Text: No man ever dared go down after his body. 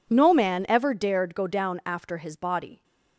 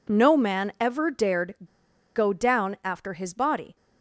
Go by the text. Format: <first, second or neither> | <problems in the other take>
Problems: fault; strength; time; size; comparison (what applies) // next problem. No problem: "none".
first | pauses between "dared" and "go"; noticeable; at 1.5 s; 0.60 s long